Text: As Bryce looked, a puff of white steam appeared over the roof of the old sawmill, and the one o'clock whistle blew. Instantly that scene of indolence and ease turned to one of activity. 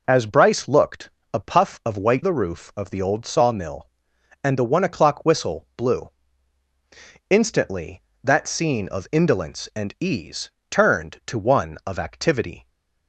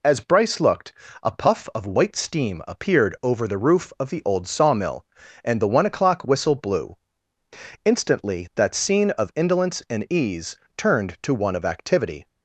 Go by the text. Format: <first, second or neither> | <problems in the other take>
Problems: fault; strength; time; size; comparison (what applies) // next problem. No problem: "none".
second | skips "steam appeared over"; at 2.2 s // pauses between "ease" and "turned"; slight; at 10.5 s; 0.18 s long; slight in the second